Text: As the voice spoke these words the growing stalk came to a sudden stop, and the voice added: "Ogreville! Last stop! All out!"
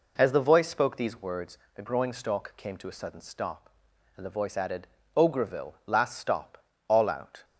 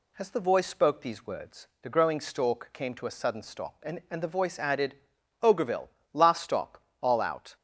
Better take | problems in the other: first | pauses between "words" and "the"; slight; at 1.6 s; 0.16 s long; slight in the first // says "and" twice; at 4.1 s

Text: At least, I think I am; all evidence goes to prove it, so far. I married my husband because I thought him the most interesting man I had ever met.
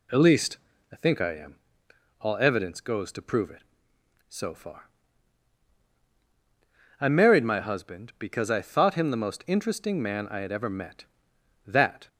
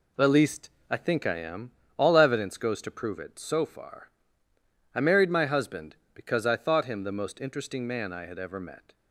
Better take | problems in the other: second | goes on to say "That"; slight; from 11.6 s on; 0.44 s long

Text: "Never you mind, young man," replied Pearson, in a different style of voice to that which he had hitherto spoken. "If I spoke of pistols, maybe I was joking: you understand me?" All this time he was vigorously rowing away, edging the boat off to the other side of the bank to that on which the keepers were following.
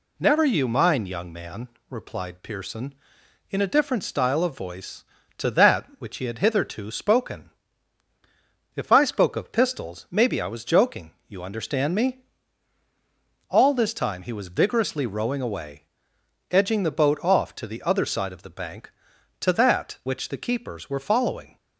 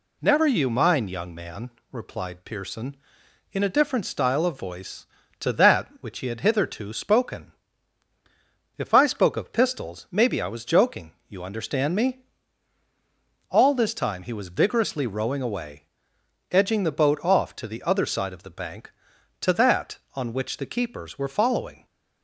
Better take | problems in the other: second | skips "on"; at 20.0 s

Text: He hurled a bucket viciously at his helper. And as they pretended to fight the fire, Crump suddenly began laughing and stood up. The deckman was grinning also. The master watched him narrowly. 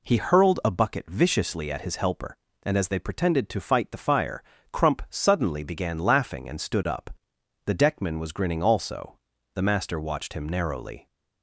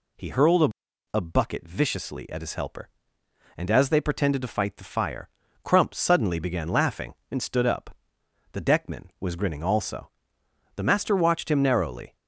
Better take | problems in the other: first | says "a" twice; at 1.1 s

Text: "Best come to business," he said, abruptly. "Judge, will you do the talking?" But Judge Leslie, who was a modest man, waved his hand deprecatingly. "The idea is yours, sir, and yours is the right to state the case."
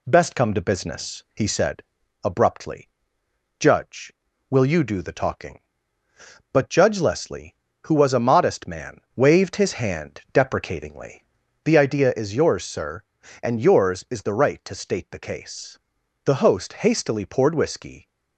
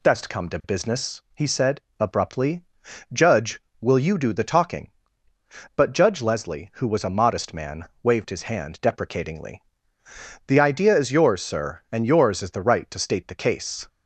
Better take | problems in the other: second | goes on to say "The host hastily poured whiskey"; strong; from 16.2 s on; 1.8 s long

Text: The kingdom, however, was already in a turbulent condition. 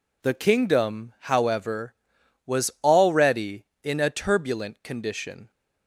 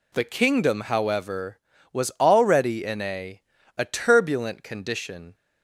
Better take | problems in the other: first | says "a" twice; at 3.7 s

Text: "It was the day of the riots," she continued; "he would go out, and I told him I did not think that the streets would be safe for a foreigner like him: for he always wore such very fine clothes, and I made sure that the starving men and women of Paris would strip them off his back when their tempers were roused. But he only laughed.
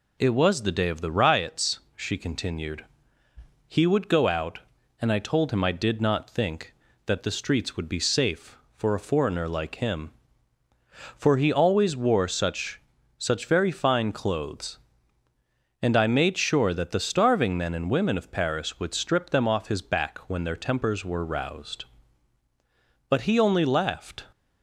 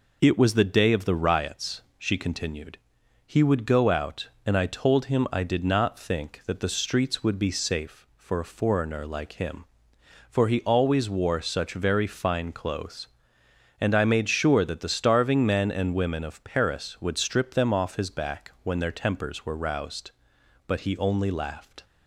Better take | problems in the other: second | says "such" twice; at 13.1 s

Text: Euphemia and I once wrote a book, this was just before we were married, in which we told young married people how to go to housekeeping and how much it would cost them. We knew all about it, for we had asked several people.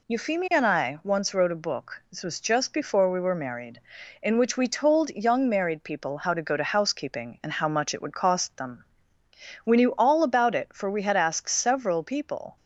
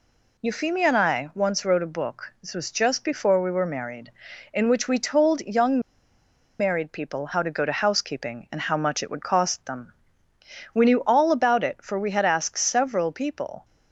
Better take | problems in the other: first | pauses between "young" and "married"; noticeable; at 5.7 s; 0.80 s long

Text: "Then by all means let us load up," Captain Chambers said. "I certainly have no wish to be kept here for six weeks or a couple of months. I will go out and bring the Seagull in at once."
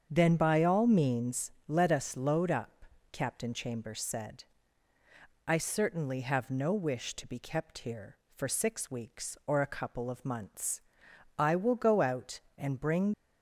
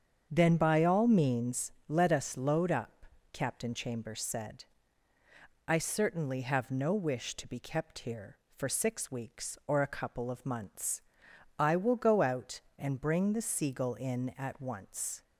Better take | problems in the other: second | starts louder than the rest; strong; until 1.1 s; 7.5 dB; strong in the second // pauses between "means" and "let"; slight; at 1.5 s; 0.16 s long; slight in the second // stops before "the Seagull in at once"; at 13.1 s

